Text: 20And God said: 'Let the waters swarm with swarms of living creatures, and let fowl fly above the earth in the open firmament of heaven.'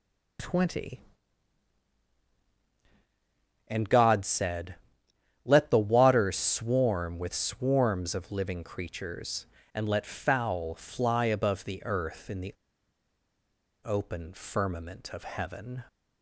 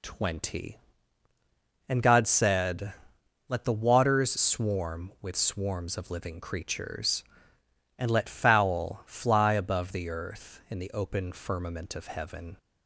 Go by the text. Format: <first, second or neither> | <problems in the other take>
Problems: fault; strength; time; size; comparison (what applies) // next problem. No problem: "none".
second | pauses between "the" and "open"; strong; at 12.5 s; 1.2 s long